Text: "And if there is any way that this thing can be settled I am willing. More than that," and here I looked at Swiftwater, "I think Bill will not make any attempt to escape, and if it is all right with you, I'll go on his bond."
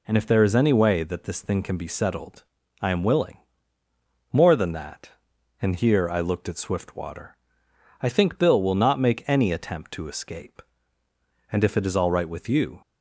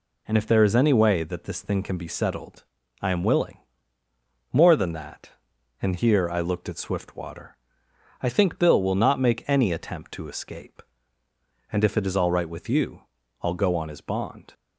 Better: second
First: pauses between "settled" and "I"; at 2.4 s; 0.40 s long // stops before "I'll go on his bond"; at 12.8 s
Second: pauses between "settled" and "I"; at 2.6 s; 0.40 s long

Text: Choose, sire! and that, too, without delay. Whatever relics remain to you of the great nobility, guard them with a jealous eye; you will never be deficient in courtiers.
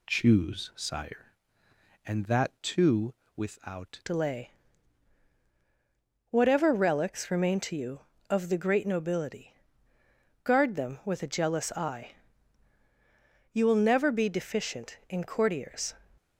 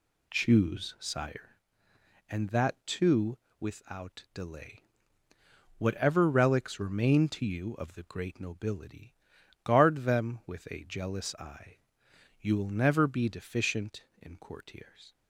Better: second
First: changes voice at "delay"; from 4.0 s on; 11.9 s long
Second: none

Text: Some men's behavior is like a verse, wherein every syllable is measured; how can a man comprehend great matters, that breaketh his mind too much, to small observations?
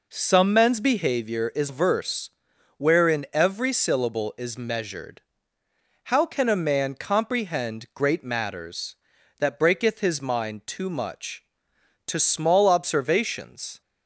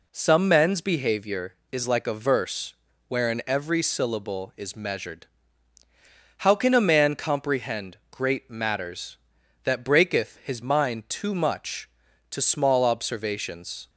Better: second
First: skips "like a"; at 1.6 s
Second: none

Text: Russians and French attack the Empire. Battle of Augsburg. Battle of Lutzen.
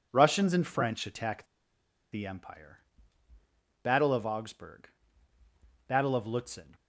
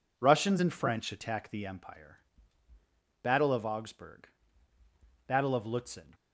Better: second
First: pauses between "attack" and "the"; noticeable; at 1.4 s; 0.67 s long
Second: none

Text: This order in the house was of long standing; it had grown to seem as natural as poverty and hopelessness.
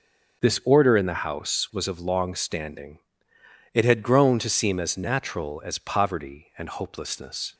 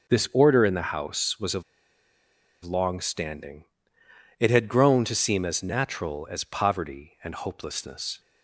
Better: first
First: starts louder than the rest; until 1.4 s; 6 dB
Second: starts louder than the rest; until 1.1 s; 6 dB // pauses between "of" and "long"; at 1.6 s; 1.0 s long

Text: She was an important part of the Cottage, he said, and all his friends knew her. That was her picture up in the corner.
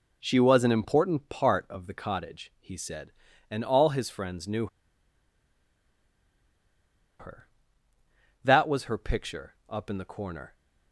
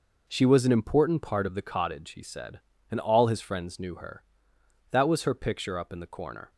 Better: second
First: pauses between "knew" and "her"; strong; at 4.6 s; 2.5 s long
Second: none

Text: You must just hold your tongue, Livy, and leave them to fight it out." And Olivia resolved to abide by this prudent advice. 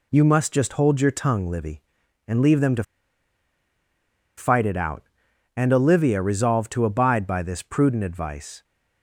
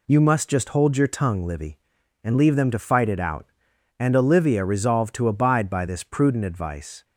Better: second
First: pauses between "to" and "fight"; strong; at 2.8 s; 1.5 s long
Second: none

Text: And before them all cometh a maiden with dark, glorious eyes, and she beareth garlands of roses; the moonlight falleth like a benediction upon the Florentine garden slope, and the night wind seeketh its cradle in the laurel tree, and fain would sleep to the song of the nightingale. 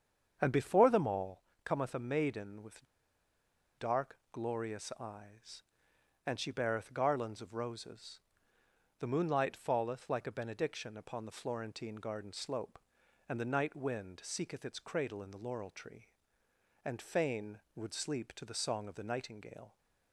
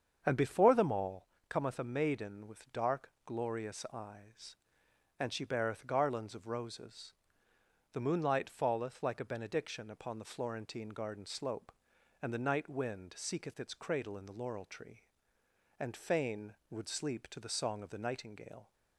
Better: second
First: starts louder than the rest; strong; until 1.4 s; 7.5 dB // pauses between "all" and "cometh"; slight; at 1.4 s; 0.22 s long // pauses between "with" and "dark"; noticeable; at 2.8 s; 0.93 s long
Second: starts louder than the rest; strong; until 1.2 s; 7.5 dB // pauses between "all" and "cometh"; slight; at 1.2 s; 0.22 s long

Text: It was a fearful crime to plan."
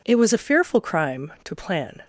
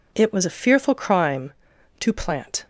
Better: first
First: none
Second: says "plant" for "plan"; at 2.1 s

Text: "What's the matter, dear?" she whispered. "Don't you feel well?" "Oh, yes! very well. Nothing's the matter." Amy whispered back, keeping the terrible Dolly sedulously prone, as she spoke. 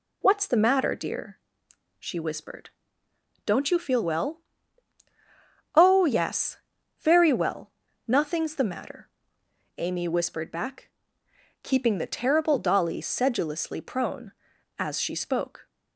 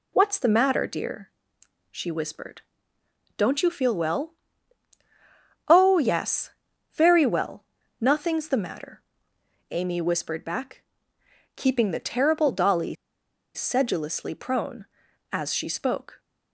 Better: first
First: none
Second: pauses between "Dolly" and "sedulously"; noticeable; at 12.9 s; 0.60 s long

